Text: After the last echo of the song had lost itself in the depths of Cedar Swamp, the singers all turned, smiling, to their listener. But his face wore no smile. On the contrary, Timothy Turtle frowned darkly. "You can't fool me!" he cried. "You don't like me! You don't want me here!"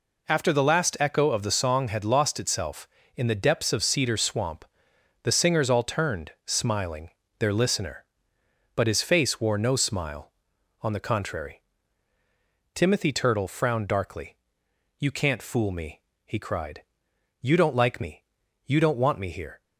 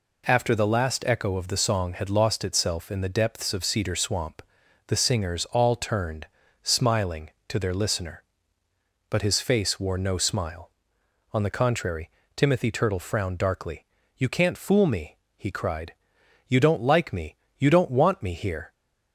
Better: second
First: skips "to"; at 7.2 s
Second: none

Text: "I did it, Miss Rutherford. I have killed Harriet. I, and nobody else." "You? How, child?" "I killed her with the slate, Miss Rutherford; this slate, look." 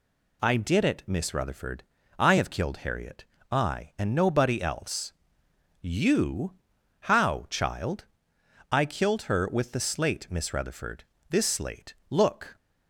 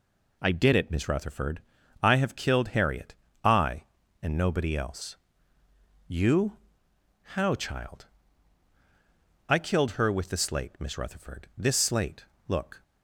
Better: neither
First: none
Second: none

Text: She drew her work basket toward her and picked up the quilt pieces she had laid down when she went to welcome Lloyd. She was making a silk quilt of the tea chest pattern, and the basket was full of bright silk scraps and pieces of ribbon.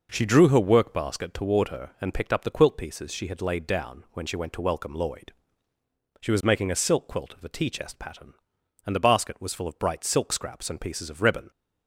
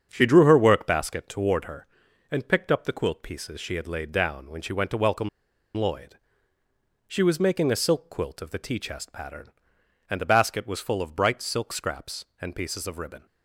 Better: first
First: none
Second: starts louder than the rest; strong; until 1.1 s; 7.5 dB // pauses between "welcome" and "Lloyd"; noticeable; at 5.2 s; 0.48 s long

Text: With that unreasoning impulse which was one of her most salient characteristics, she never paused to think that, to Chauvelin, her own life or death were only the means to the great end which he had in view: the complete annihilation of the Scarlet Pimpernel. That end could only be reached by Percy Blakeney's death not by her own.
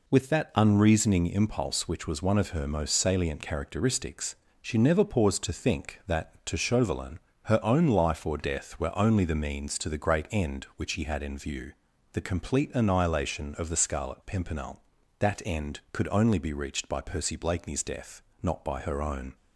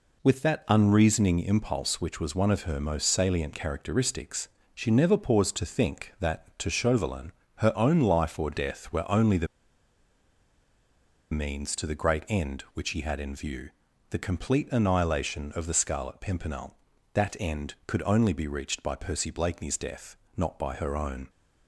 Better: first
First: pauses between "death" and "not"; slight; at 18.2 s; 0.18 s long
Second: pauses between "the" and "means"; strong; at 9.4 s; 1.8 s long // pauses between "death" and "not"; slight; at 20.1 s; 0.18 s long

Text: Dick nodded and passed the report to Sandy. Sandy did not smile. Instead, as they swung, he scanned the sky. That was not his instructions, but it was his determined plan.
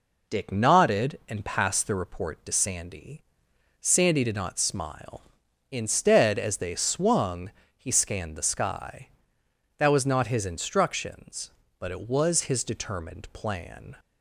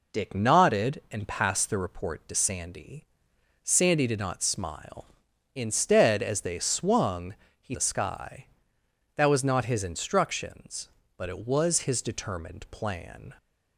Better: first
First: none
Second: skips "scanned"; at 7.7 s

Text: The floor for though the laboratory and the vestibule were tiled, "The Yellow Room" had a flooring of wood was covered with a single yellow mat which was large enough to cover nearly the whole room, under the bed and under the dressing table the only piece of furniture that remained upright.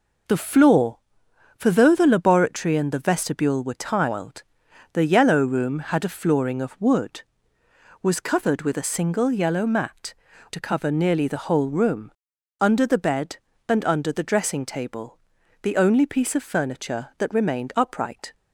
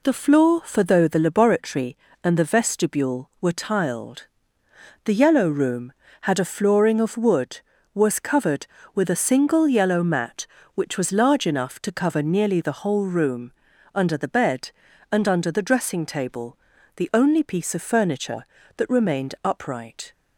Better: second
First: skips "which was large enough"; at 10.3 s // pauses between "table" and "the"; noticeable; at 15.1 s; 0.46 s long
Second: pauses between "table" and "the"; at 16.5 s; 0.40 s long

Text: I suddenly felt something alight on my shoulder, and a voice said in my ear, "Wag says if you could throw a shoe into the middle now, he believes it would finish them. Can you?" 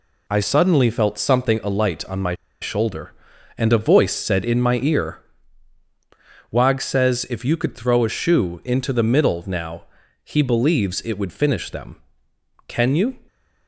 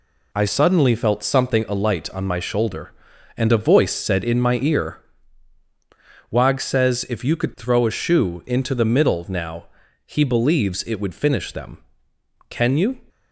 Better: second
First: pauses between "my" and "shoulder"; slight; at 2.3 s; 0.26 s long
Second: none

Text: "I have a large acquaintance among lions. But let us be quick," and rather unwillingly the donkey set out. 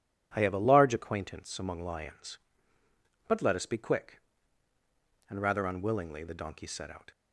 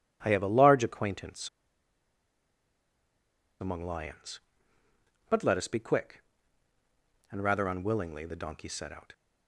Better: first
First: none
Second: pauses between "acquaintance" and "among"; strong; at 1.4 s; 2.1 s long

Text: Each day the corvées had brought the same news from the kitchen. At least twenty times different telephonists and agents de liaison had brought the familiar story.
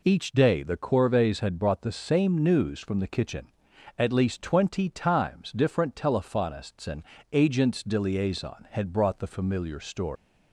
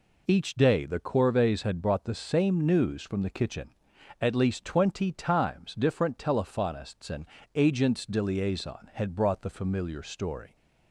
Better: second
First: pauses between "and" and "agents"; slight; at 7.0 s; 0.28 s long // leaves "story" unfinished; at 10.1 s; 170 ms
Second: pauses between "and" and "agents"; slight; at 7.2 s; 0.28 s long

